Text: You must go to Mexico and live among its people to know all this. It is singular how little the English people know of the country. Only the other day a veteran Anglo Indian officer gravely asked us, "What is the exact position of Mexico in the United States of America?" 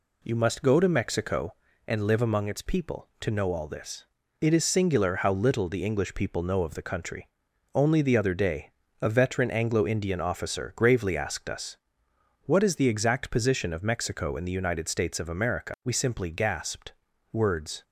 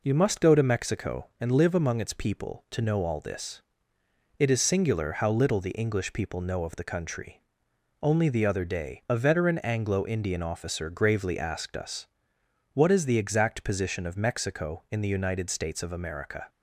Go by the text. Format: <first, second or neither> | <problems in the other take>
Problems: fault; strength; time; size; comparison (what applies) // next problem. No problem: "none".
second | pauses between "day" and "a"; slight; at 8.6 s; 0.34 s long // goes on to say "We simply gasped words"; strong; from 15.8 s on; 1.9 s long